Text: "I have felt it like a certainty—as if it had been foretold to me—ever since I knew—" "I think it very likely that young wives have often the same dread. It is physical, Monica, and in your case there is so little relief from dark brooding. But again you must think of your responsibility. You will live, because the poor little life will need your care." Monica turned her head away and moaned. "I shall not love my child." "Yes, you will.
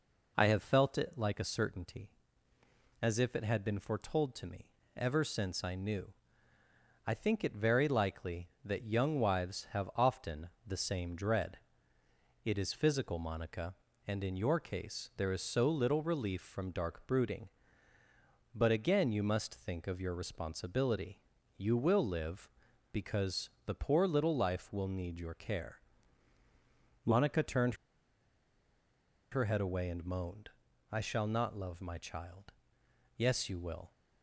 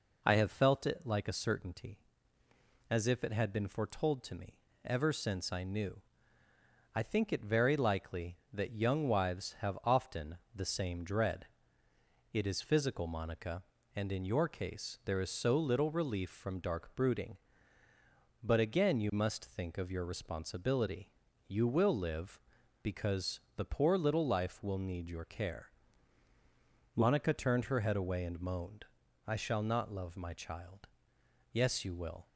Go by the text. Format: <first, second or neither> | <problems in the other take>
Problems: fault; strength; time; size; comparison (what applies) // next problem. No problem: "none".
second | pauses between "often" and "the"; slight; at 10.4 s; 0.16 s long; slight in the second // pauses between "turned" and "her"; strong; at 27.7 s; 1.5 s long